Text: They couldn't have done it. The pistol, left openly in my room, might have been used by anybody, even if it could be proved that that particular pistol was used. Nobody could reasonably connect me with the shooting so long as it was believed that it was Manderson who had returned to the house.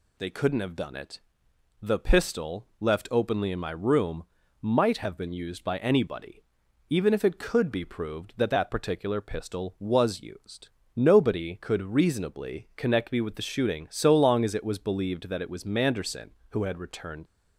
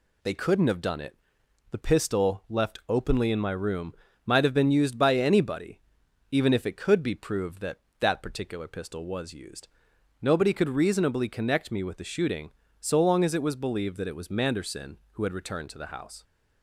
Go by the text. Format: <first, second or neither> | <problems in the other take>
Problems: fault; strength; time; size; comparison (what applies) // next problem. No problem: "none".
second | stops before "to the house"; at 17.2 s